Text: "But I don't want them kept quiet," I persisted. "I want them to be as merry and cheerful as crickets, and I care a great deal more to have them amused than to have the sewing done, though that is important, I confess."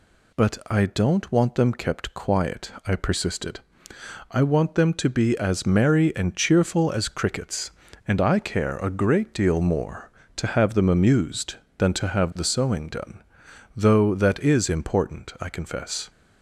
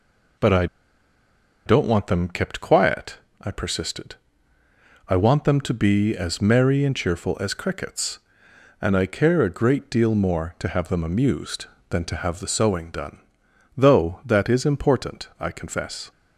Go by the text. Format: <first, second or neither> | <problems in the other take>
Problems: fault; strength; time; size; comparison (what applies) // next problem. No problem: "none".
first | pauses between "I" and "don't"; at 0.6 s; 1.0 s long